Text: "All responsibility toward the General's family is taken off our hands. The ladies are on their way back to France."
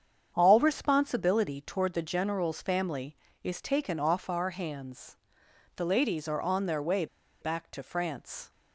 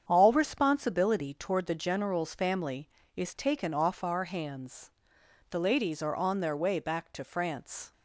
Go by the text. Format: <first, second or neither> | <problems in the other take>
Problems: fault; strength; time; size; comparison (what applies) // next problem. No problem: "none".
second | starts louder than the rest; strong; until 1.3 s; 7.5 dB; strong in the second // pauses between "way" and "back"; slight; at 7.0 s; 0.35 s long